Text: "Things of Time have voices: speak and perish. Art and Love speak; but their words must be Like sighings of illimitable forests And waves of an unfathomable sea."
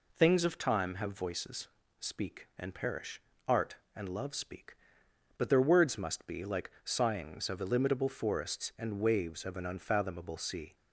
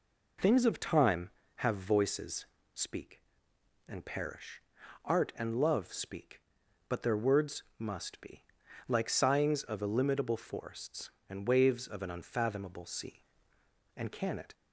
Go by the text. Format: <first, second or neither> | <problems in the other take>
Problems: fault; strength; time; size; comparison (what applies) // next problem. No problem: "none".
first | pauses between "be" and "Like"; at 8.4 s; 0.42 s long // goes on to say "And can it"; from 13.9 s on; 0.56 s long